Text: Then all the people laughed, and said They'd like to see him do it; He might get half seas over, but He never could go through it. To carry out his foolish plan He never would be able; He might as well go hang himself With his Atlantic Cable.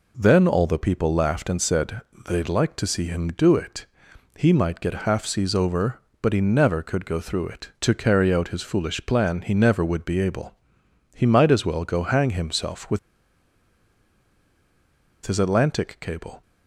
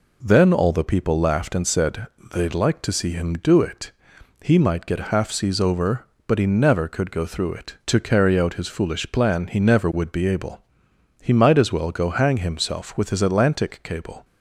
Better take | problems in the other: second | pauses between "said" and "They'd"; slight; at 1.9 s; 0.28 s long; slight in the second // pauses between "With" and "his"; strong; at 12.9 s; 2.2 s long

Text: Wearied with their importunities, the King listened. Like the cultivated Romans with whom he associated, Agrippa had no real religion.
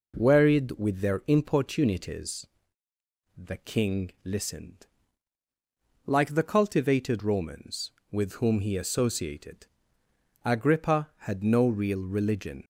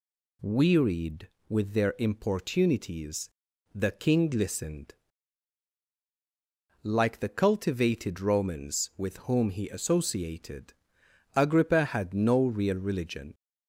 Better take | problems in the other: neither | none

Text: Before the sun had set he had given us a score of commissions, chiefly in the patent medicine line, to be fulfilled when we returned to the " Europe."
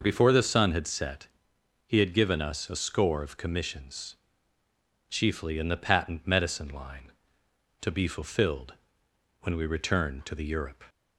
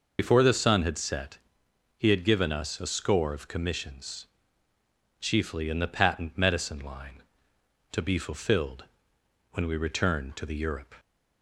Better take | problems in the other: first | loses the start of "Before"; at 0.1 s; 75 ms // pauses between "set" and "he"; noticeable; at 1.3 s; 0.58 s long; noticeable in the first // pauses between "fulfilled" and "when"; noticeable; at 8.8 s; 0.68 s long; noticeable in the first

